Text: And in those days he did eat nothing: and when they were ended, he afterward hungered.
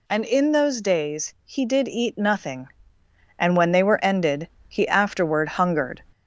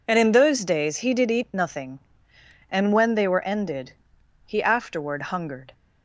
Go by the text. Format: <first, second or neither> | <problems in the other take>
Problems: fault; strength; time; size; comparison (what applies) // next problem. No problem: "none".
second | gets louder; slight; throughout; 3 dB